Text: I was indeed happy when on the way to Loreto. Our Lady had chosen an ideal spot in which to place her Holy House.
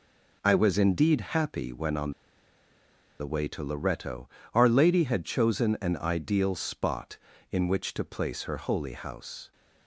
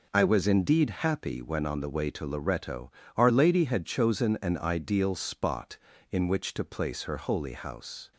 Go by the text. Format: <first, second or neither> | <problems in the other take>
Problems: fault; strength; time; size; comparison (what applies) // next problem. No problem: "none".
second | pauses between "on" and "the"; at 2.1 s; 1.0 s long